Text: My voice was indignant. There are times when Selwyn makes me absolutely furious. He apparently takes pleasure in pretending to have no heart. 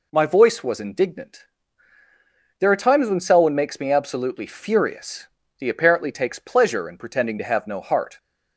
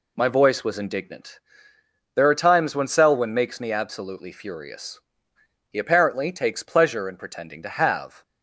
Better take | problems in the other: first | stops before "no heart"; at 8.2 s

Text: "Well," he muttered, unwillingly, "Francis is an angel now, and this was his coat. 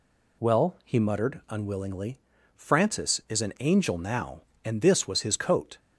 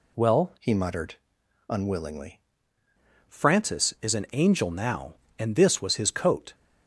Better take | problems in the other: first | changes voice from "he" to "unwillingly"; from 0.5 to 2.3 s; 1.8 s long

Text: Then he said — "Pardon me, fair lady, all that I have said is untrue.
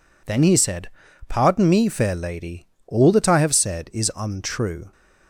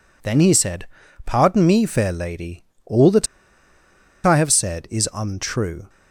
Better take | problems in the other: first | pauses between "that" and "I"; at 3.2 s; 0.98 s long

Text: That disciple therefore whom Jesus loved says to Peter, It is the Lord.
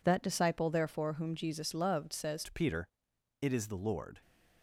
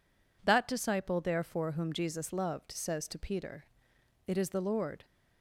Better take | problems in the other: second | changes voice at "to"; from 2.4 s on; 1.8 s long

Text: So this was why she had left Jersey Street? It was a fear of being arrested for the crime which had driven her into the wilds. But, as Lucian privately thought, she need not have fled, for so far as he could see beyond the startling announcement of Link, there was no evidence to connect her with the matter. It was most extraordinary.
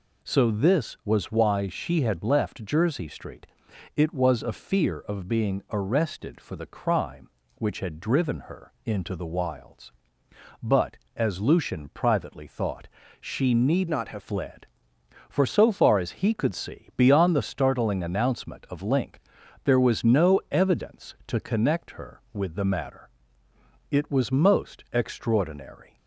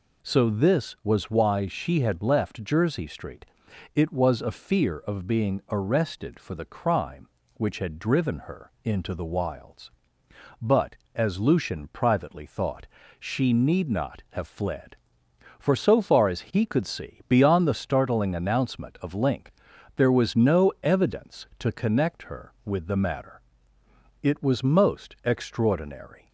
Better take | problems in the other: second | changes voice from "not" to "have"; from 13.8 to 14.2 s; 0.4 s long

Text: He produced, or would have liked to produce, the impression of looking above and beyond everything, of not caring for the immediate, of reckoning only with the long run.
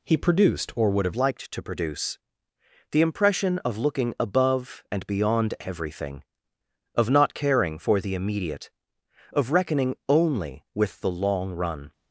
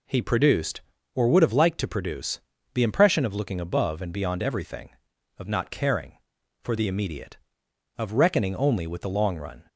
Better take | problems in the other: second | changes voice at "liked"; from 1.1 s on; 10.8 s long

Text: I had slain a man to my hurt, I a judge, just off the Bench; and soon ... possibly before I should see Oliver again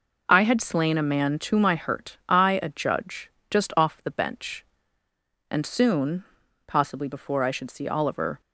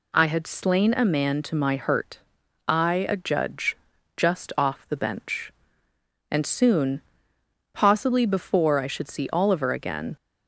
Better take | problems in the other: second | stops before "again"; at 8.4 s

